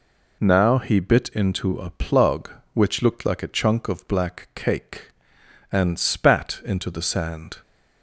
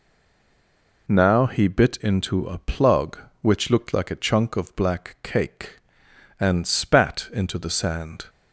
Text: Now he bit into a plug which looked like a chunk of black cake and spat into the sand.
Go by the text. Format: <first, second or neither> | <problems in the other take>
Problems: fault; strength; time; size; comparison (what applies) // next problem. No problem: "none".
first | stays silent before the first word; until 1.0 s; 1.0 s long